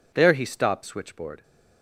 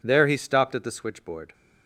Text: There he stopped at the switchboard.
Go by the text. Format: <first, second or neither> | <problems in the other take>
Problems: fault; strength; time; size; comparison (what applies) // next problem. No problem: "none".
second | skips "at the"; at 0.8 s